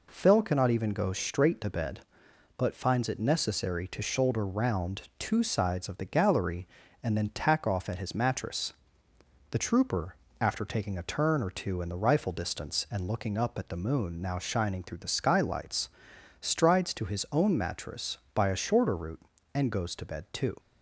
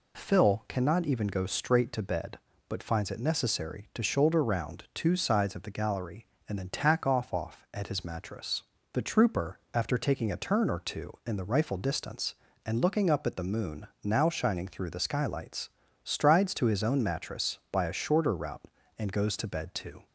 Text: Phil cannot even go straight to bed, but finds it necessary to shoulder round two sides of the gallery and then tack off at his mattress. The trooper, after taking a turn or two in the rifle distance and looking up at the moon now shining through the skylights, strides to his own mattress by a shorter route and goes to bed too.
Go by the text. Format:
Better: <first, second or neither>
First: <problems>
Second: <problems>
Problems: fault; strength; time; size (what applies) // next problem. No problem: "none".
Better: first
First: none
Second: says "off" twice; at 7.3 s